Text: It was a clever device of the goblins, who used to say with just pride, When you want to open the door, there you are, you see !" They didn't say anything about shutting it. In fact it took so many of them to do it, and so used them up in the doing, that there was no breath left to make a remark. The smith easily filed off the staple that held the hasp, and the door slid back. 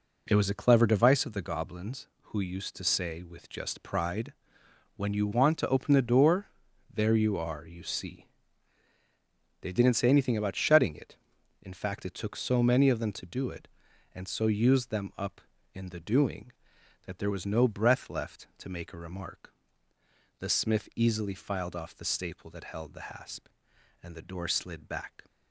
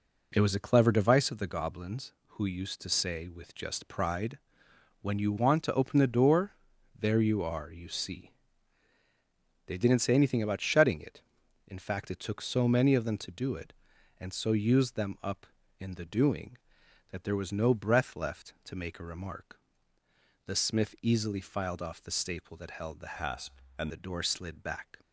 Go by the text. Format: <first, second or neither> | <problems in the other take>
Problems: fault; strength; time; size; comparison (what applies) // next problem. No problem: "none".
first | changes voice from "hasp" to "and"; from 23.1 to 23.8 s; 0.7 s long